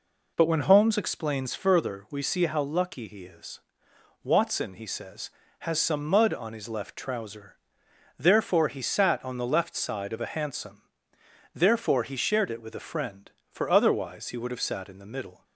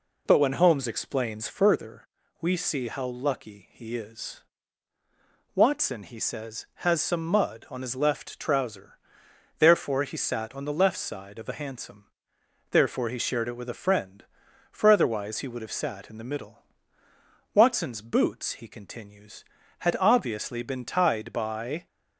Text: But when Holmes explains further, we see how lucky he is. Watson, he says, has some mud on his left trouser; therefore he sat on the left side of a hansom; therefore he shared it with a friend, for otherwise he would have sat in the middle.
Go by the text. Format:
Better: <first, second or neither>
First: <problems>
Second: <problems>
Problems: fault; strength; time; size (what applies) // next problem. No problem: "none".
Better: first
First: none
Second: goes on to say "Watson's boots he continues had obviously been tied by"; strong; from 17.5 s on; 4.3 s long